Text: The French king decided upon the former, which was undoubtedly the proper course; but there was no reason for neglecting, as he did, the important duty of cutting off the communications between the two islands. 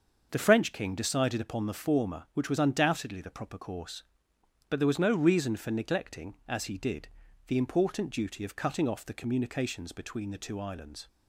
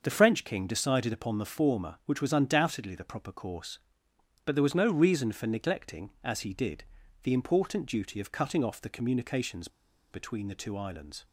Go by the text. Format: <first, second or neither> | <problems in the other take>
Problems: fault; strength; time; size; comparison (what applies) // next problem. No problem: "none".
first | starts louder than the rest; until 1.0 s; 6.5 dB; also in the first // pauses between "communications" and "between"; at 9.6 s; 0.44 s long